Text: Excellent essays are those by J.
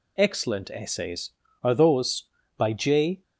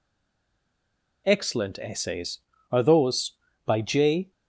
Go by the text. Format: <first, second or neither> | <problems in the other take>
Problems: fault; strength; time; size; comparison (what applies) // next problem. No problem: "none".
first | stays silent before the first word; noticeable; until 1.2 s; 1.2 s long